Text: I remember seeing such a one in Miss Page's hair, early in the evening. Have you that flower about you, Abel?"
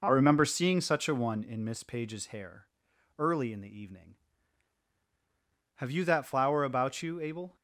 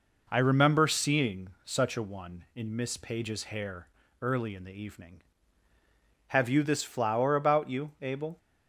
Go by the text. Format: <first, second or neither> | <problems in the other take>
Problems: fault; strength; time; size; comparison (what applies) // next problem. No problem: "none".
first | pauses between "seeing" and "such"; slight; at 1.4 s; 0.16 s long // says "this" for "that"; at 6.6 s